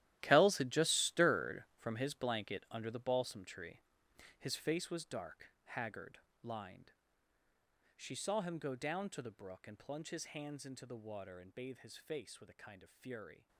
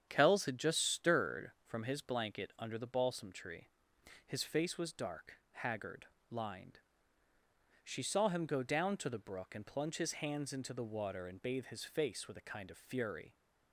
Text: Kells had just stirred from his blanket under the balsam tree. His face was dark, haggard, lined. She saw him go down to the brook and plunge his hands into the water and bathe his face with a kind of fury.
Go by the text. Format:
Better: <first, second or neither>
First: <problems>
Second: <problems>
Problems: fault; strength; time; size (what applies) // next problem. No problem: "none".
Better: second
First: gets quieter; strong; throughout; 15.5 dB // starts louder than the rest; strong; until 1.2 s; 13.5 dB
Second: starts louder than the rest; strong; until 1.1 s; 8.5 dB